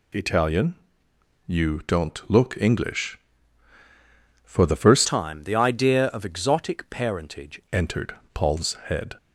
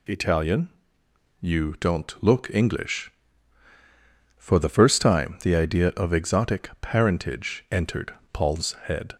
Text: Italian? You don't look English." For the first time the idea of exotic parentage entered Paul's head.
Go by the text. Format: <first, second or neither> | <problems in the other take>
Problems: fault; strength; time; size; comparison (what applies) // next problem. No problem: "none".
second | changes voice from "time" to "parentage"; from 5.0 to 7.6 s; 2.6 s long // pauses between "entered" and "Paul's"; slight; at 8.1 s; 0.18 s long; slight in the second